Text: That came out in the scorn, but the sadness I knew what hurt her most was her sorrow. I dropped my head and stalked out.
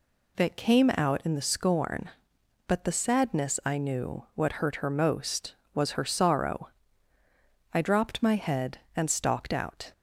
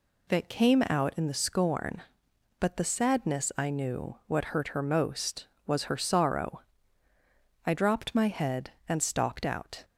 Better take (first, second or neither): neither